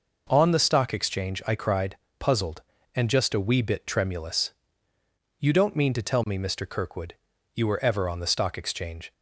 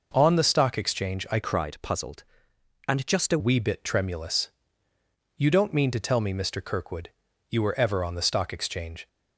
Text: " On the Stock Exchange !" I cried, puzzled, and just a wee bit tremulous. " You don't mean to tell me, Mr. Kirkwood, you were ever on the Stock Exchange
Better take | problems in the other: first | changes voice from "cried" to "a"; from 1.4 to 3.3 s; 1.9 s long

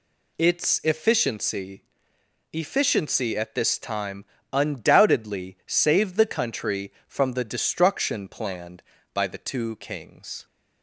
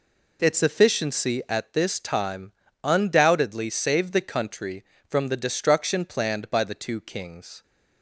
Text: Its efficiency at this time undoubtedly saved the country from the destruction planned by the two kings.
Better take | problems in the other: second | says "efficiency" twice; at 2.5 s // pauses between "time" and "undoubtedly"; slight; at 4.2 s; 0.26 s long; slight in the second

